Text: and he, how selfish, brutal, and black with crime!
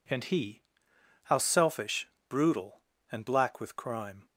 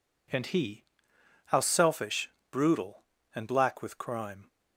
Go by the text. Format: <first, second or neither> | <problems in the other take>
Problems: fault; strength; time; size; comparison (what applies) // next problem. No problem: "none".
neither | none